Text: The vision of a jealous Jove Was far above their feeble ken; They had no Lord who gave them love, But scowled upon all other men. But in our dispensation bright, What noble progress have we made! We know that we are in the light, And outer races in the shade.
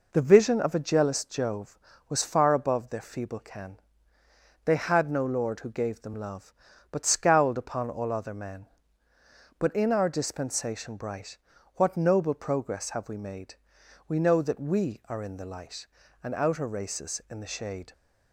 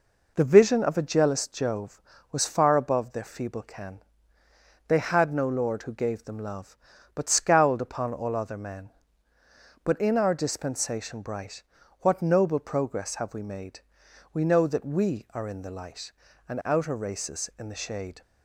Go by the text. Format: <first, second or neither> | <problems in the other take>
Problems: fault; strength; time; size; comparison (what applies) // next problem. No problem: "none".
neither | none